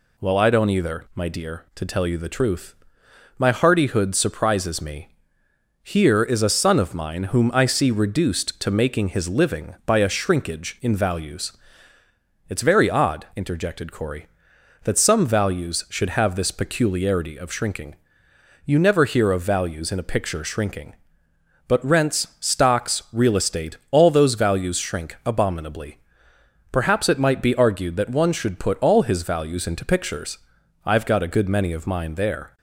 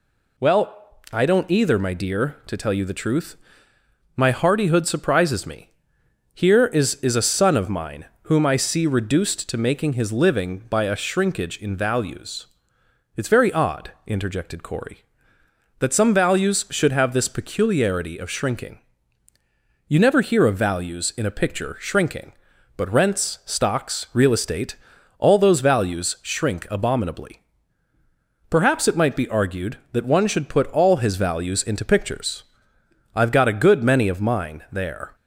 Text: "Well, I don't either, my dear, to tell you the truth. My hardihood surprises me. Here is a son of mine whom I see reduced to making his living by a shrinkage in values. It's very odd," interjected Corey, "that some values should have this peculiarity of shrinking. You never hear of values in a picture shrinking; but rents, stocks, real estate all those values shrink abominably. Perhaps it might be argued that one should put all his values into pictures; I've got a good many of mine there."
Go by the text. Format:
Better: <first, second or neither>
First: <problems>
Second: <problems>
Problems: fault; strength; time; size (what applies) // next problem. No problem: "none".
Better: first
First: none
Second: says "is" twice; at 6.9 s // pauses between "mine" and "whom"; slight; at 8.0 s; 0.16 s long // pauses between "estate" and "all"; at 24.7 s; 0.42 s long